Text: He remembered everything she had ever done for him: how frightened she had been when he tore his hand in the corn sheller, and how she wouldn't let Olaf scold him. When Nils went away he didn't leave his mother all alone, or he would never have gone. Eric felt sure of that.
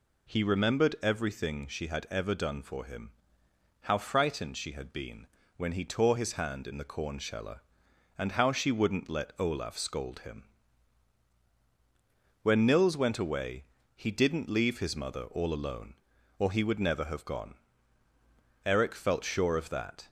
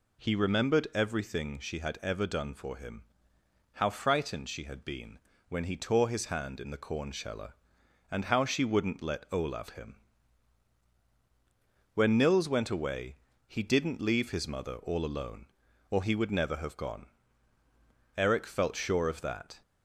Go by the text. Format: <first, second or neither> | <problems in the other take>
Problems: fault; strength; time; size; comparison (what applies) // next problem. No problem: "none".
first | pauses between "been" and "when"; slight; at 5.1 s; 0.30 s long; slight in the first // skips "scold"; at 9.7 s // pauses between "away" and "he"; slight; at 13.1 s; 0.32 s long; slight in the first